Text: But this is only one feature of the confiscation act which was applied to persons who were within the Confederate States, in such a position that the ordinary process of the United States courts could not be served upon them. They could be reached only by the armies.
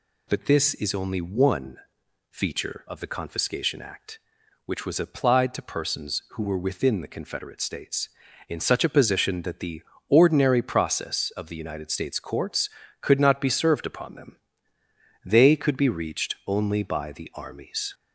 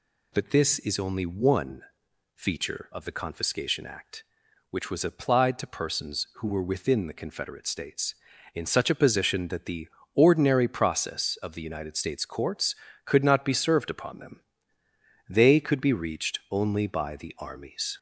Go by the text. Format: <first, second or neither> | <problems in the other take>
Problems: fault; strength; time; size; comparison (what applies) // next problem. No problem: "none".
neither | pauses between "one" and "feature"; noticeable; the same in both // pauses between "the" and "ordinary"; slight; the same in both